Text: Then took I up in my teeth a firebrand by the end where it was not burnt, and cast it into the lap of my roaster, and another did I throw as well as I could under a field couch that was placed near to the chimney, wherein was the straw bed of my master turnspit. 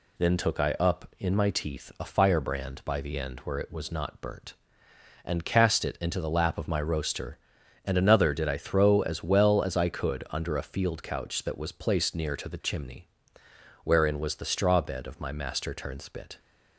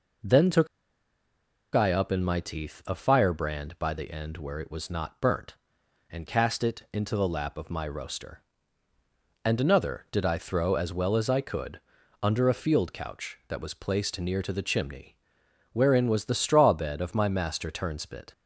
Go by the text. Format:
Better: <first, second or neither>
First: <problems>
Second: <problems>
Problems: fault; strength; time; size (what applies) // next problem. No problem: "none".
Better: first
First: none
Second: pauses between "took" and "I"; at 0.6 s; 1.0 s long // pauses between "could" and "under"; at 11.8 s; 0.42 s long